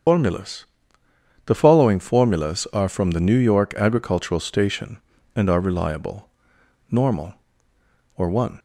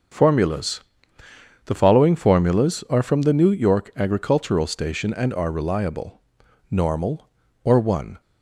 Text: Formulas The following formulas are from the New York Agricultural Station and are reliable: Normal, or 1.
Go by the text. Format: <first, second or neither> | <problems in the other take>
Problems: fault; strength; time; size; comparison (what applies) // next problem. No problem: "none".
second | loses the start of "Formulas"; at 0.0 s; 105 ms // starts louder than the rest; strong; until 1.8 s; 7.5 dB; also in the second // pauses between "Formulas" and "The"; noticeable; at 0.6 s; 0.80 s long; noticeable in the second